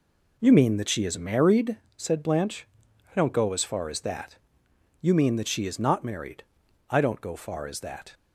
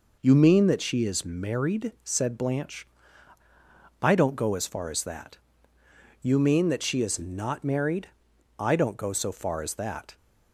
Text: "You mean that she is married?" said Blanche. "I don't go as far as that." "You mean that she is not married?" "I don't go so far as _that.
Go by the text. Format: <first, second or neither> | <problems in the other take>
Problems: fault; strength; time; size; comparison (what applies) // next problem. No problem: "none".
second | skips "so"; at 7.3 s